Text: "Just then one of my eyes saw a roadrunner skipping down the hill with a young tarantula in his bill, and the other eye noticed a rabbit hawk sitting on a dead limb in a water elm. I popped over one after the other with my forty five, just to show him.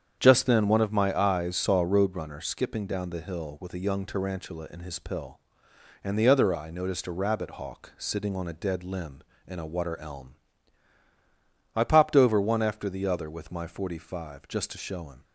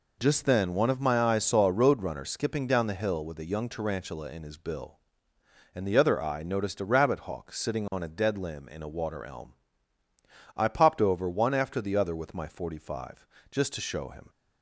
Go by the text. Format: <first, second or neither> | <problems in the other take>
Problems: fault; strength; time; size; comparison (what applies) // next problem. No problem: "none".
second | starts louder than the rest; strong; until 1.2 s; 8 dB // says "pill" for "bill"; at 4.9 s